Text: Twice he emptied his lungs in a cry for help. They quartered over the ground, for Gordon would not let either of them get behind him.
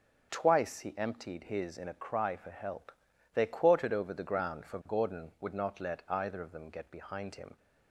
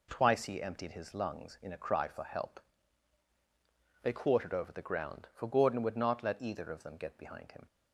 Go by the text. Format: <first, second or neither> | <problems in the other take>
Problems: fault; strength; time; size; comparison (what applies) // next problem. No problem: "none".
second | starts louder than the rest; until 1.3 s; 6.5 dB // skips "lungs"; at 1.7 s